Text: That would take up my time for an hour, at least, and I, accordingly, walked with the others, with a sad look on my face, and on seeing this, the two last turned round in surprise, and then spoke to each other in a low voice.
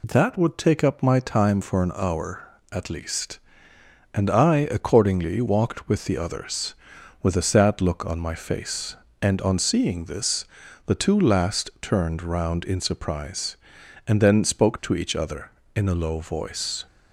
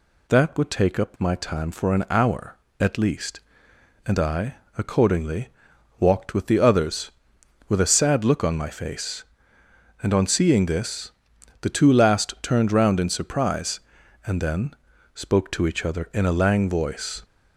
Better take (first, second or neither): first